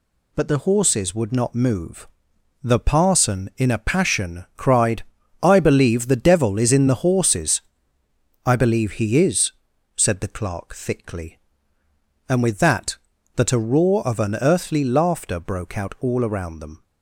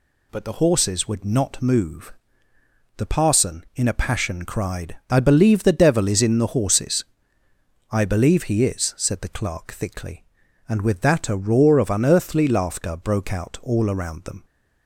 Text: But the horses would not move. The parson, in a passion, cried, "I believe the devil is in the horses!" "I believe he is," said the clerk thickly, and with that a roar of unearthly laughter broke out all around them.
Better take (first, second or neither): second